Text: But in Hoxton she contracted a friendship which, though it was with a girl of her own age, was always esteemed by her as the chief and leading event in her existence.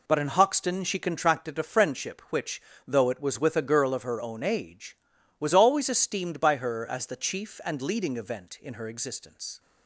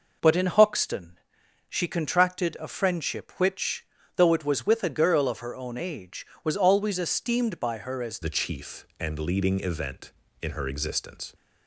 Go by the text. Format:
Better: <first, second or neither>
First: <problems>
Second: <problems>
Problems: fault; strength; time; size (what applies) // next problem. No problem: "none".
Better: first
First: none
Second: pauses between "Hoxton" and "she"; noticeable; at 1.1 s; 0.50 s long // changes voice at "the"; from 8.2 s on; 3.1 s long